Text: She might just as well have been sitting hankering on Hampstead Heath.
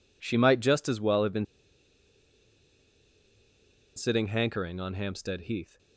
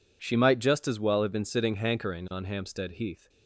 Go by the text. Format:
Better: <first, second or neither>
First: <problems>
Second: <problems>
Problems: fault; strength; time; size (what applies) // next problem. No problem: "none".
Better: second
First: pauses between "been" and "sitting"; strong; at 1.4 s; 2.5 s long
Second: none